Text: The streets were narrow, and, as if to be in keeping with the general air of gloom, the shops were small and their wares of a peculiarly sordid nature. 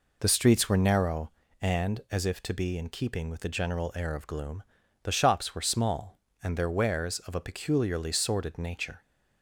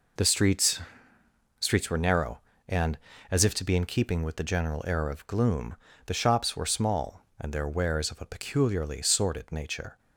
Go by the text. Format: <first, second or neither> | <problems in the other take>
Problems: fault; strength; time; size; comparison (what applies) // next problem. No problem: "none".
first | says "streets" twice; at 1.5 s